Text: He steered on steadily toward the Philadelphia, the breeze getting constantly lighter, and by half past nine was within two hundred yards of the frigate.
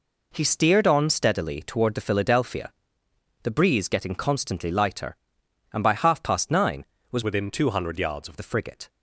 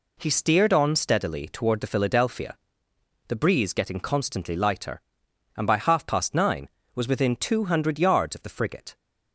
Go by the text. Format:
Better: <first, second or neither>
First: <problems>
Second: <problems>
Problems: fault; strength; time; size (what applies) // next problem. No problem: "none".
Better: second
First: changes voice from "within" to "of"; from 7.2 to 8.3 s; 1.1 s long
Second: none